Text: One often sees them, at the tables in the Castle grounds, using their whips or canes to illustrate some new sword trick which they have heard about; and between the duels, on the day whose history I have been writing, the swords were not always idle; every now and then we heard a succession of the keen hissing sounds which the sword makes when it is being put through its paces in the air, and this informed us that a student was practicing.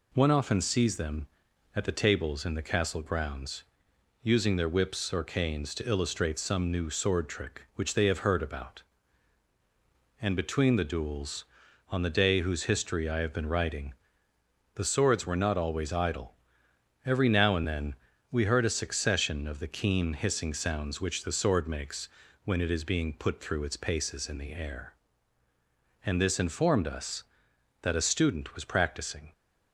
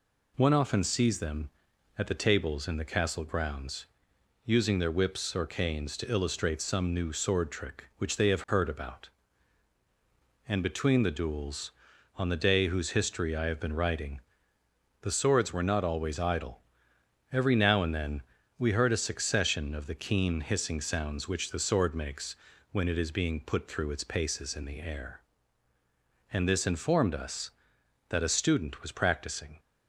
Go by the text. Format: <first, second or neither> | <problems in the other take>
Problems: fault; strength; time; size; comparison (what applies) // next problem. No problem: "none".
neither | pauses between "then" and "we"; slight; the same in both // pauses between "makes" and "when"; slight; the same in both